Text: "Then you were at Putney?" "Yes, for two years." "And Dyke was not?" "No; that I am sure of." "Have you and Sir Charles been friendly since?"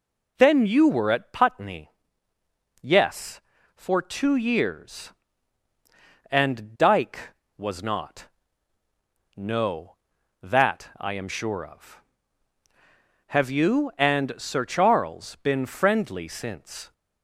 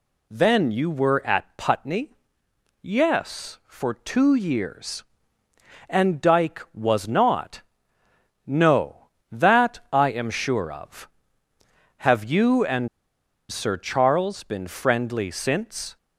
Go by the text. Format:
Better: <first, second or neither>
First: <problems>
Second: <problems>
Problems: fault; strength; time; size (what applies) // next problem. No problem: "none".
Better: first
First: none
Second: pauses between "and" and "Sir"; noticeable; at 12.8 s; 0.62 s long